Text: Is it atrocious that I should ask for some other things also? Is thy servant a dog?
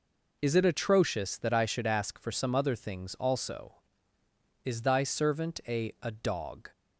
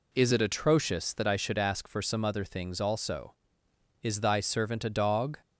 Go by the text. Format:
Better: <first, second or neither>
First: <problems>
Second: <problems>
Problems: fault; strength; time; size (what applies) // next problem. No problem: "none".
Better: second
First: says "a" twice; at 6.0 s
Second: none